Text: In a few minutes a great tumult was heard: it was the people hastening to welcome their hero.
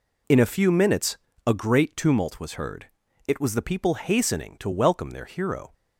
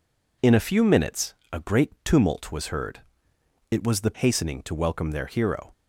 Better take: first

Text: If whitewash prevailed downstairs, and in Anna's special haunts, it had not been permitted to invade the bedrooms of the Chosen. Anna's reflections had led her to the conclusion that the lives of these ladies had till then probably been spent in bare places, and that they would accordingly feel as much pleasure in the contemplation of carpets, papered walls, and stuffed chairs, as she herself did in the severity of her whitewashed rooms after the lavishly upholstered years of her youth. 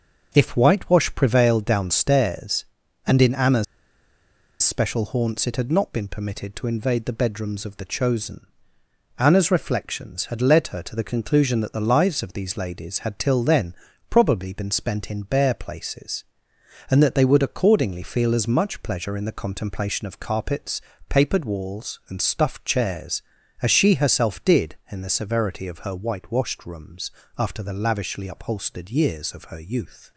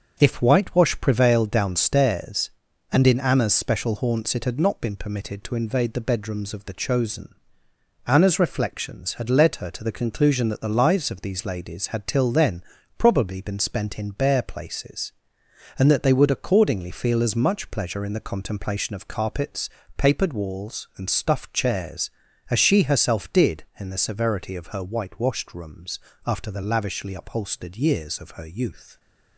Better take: second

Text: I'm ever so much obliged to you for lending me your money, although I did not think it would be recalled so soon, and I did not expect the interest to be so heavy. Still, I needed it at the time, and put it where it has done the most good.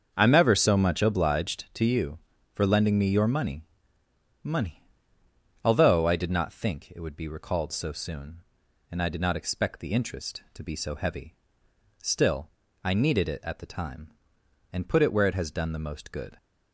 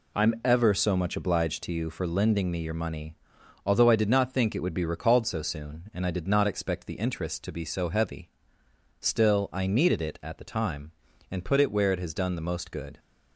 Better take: second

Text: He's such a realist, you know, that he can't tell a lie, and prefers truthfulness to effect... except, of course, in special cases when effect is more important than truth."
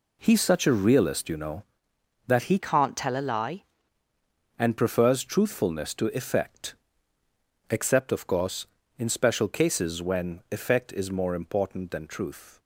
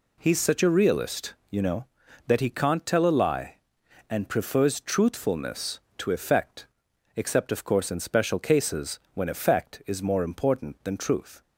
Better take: second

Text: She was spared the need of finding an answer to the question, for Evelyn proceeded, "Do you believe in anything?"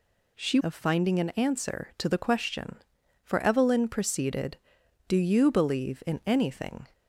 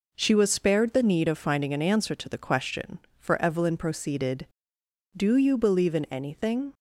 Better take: second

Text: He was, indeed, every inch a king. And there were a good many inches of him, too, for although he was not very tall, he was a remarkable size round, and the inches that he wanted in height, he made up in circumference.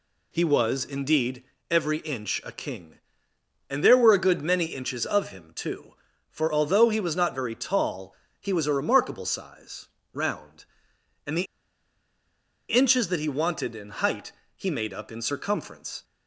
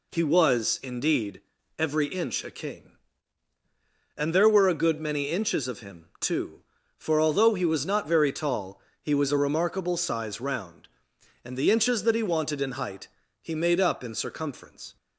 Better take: second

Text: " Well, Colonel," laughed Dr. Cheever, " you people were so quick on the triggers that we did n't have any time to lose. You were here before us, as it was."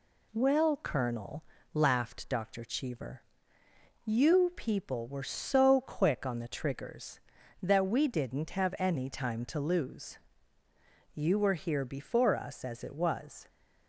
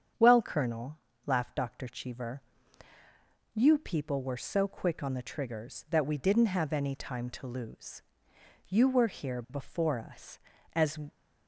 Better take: first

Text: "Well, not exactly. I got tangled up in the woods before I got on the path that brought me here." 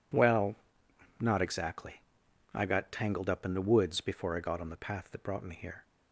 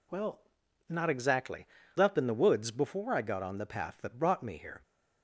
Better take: first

